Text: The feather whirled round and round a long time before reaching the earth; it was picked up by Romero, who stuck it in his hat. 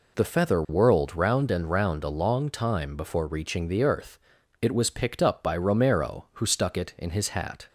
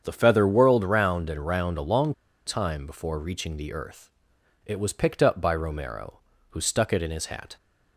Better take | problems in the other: first | starts louder than the rest; strong; until 1.0 s; 7.5 dB // pauses between "long" and "time"; slight; at 2.1 s; 0.33 s long

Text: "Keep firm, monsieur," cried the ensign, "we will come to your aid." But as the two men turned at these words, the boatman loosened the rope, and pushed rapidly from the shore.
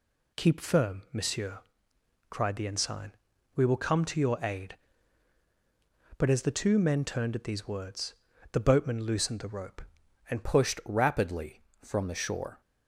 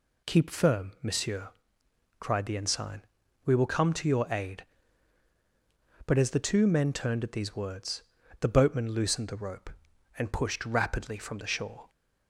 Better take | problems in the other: second | changes voice at "pushed"; from 10.4 s on; 2.2 s long

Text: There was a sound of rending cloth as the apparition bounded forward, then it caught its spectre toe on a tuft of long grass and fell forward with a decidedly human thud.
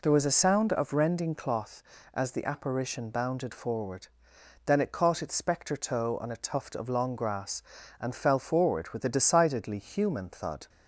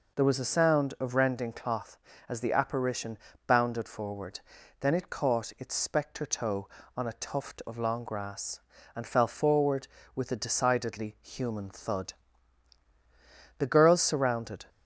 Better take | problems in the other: first | pauses between "apparition" and "bounded"; slight; at 3.1 s; 0.30 s long // goes on to say "The girls surrounded"; noticeable; from 13.5 s on; 1.0 s long

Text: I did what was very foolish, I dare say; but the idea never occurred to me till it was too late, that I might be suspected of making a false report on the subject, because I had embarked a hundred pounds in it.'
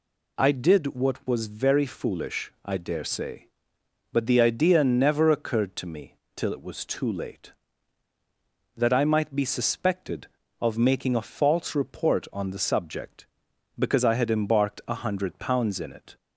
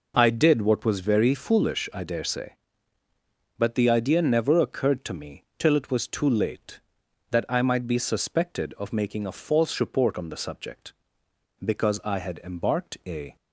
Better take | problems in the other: first | pauses between "me" and "till"; slight; at 5.4 s; 0.16 s long; slight in the first // stops before "hundred pounds in it"; at 13.3 s

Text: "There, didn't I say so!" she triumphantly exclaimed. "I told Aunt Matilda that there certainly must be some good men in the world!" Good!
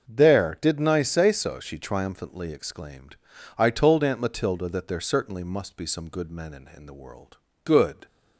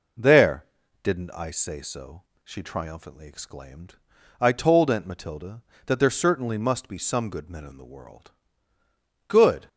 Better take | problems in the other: second | starts louder than the rest; noticeable; until 1.1 s; 6 dB // says "in" twice; at 6.7 s

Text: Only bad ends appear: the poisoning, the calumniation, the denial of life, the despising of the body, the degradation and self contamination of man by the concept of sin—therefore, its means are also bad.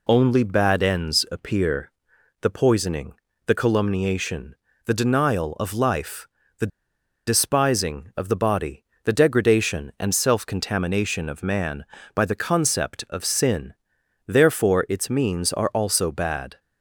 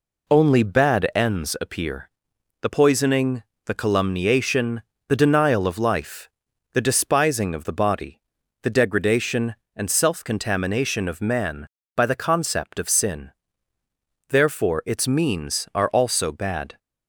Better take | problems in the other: second | pauses between "the" and "despising"; noticeable; at 6.7 s; 0.59 s long

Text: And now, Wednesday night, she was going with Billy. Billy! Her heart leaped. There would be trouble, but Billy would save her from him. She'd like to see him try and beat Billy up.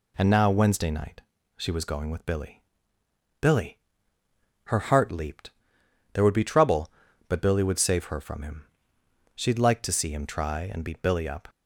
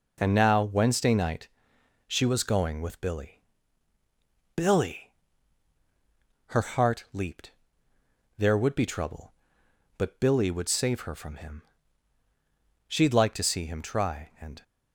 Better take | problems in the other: first | stops before "beat Billy up"; at 14.6 s

